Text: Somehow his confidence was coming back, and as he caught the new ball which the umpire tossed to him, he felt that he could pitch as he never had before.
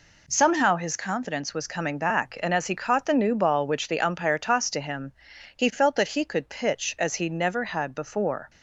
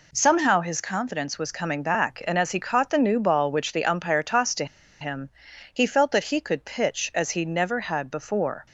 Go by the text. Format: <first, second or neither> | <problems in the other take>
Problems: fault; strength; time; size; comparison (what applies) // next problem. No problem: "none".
first | pauses between "to" and "him"; slight; at 4.6 s; 0.35 s long